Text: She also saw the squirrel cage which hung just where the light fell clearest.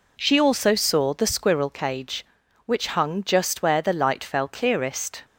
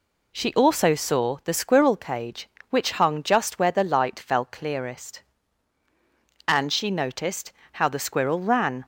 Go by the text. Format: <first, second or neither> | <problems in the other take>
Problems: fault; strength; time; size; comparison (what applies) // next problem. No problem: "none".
first | goes on to say "And she noticed how the squirrel ran"; strong; from 6.4 s on; 2.3 s long